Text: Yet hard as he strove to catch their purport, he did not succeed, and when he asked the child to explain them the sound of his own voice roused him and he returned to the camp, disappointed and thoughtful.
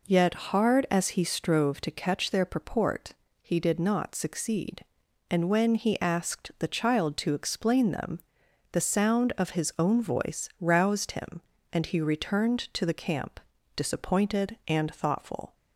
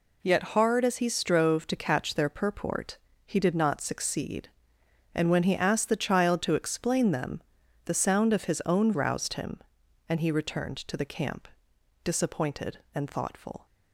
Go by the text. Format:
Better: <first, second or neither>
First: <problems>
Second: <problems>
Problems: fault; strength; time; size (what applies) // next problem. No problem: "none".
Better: first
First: pauses between "them" and "the"; noticeable; at 8.1 s; 0.54 s long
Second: pauses between "them" and "the"; at 7.4 s; 0.44 s long // skips "voice"; at 8.9 s